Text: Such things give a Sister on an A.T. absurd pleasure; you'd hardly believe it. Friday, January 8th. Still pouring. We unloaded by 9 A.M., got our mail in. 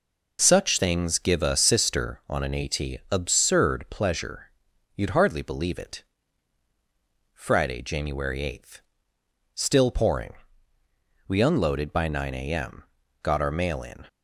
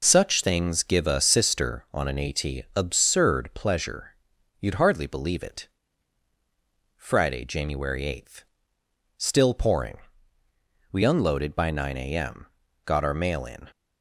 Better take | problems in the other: neither | none

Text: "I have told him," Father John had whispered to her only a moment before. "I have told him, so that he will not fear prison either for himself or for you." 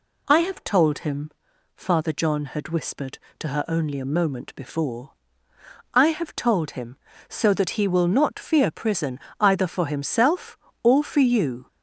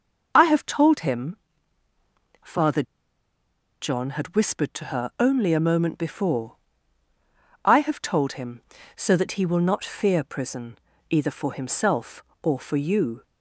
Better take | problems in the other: first | pauses between "Father" and "John"; at 2.8 s; 0.98 s long // pauses between "prison" and "either"; slight; at 10.7 s; 0.32 s long; slight in the first

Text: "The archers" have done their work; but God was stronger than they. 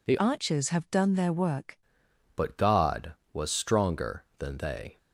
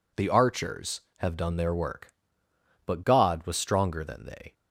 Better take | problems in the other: second | changes voice from "archers" to "work"; from 0.1 to 1.7 s; 1.6 s long

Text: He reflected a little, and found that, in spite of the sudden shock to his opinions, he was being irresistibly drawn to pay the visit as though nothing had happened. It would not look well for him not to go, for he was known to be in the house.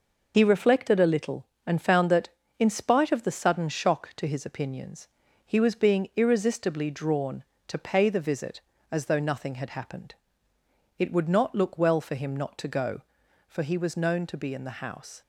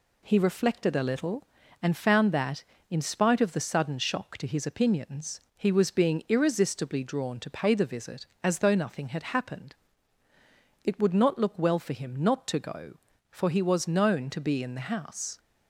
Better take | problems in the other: second | loses the start of "He"; at 0.3 s; 20 ms

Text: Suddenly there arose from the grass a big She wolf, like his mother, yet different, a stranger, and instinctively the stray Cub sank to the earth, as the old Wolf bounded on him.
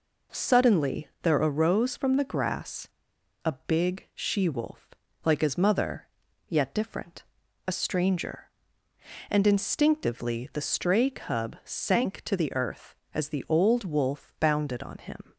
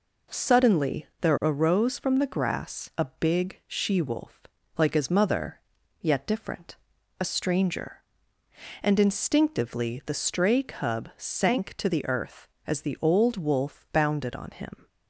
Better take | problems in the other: second | pauses between "grass" and "a"; noticeable; at 2.8 s; 0.57 s long

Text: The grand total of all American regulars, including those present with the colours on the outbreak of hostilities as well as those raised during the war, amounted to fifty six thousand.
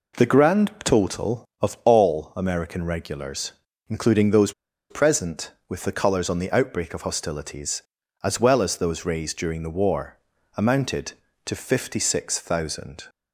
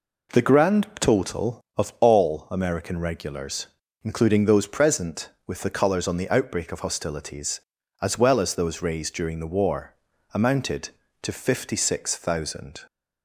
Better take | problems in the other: second | pauses between "those" and "present"; at 4.5 s; 0.37 s long

